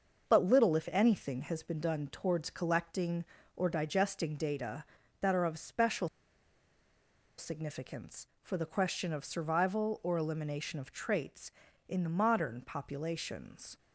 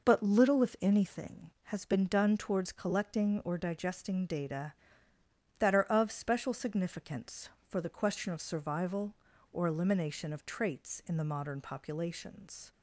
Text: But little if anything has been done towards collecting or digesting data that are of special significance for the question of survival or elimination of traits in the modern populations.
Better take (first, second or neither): second